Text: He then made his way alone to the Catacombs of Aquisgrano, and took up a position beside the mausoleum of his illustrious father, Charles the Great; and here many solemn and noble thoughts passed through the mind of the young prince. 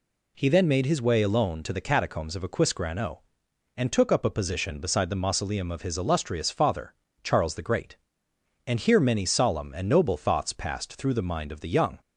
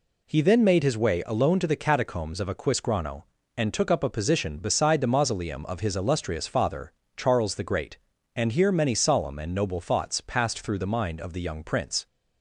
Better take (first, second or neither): second